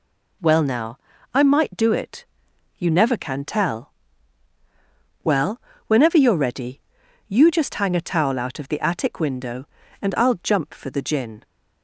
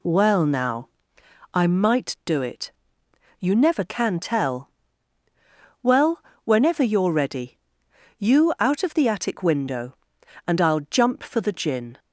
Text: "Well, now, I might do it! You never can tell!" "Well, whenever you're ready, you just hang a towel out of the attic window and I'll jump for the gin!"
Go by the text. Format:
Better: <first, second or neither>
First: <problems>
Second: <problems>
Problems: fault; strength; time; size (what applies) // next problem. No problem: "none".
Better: first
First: none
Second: skips "just hang a towel"; at 8.5 s